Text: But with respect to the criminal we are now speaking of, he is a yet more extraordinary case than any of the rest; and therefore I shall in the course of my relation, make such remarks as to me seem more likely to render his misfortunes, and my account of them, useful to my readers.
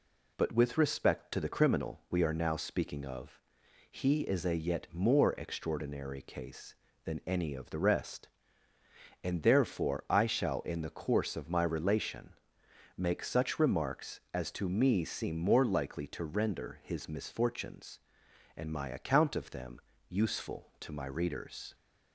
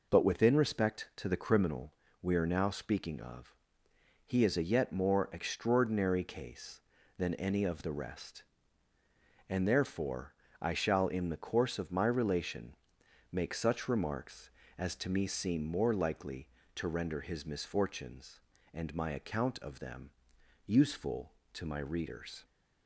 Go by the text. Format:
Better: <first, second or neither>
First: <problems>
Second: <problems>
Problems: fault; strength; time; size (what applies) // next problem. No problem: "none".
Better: first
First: none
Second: says "within" for "with"; at 0.2 s // pauses between "criminal" and "we"; slight; at 1.9 s; 0.28 s long // pauses between "therefore" and "I"; slight; at 10.3 s; 0.28 s long